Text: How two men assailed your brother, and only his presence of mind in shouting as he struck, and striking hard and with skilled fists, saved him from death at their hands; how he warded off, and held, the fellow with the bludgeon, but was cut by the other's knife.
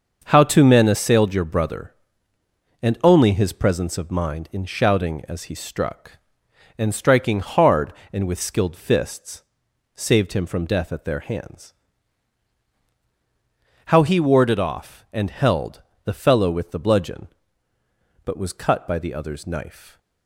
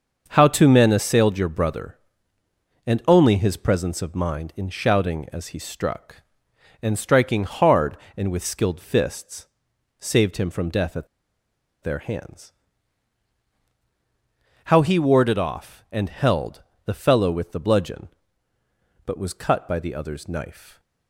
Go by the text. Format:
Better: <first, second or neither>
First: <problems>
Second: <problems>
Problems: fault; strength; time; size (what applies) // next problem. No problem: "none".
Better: first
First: starts louder than the rest; until 1.2 s; 6.5 dB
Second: starts louder than the rest; until 1.3 s; 6.5 dB // pauses between "at" and "their"; noticeable; at 11.0 s; 0.76 s long